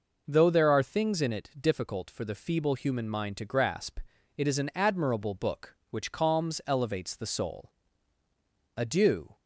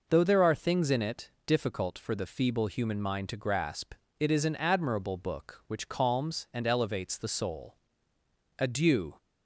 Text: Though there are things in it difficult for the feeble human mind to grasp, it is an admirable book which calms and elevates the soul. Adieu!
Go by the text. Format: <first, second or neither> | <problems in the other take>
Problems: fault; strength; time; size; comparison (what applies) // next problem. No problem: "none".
second | skips "and"; at 6.6 s